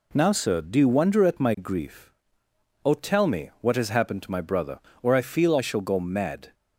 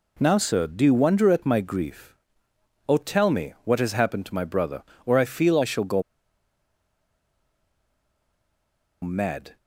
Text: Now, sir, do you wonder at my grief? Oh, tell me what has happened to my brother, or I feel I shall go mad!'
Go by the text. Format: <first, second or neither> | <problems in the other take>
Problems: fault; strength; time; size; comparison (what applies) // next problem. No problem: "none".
first | pauses between "go" and "mad"; strong; at 6.0 s; 3.0 s long